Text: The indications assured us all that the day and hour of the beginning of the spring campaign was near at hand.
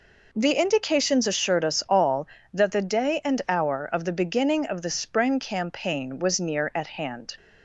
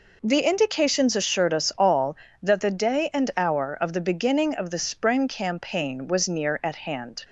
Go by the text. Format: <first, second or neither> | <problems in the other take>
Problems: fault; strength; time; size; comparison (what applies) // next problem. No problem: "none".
neither | none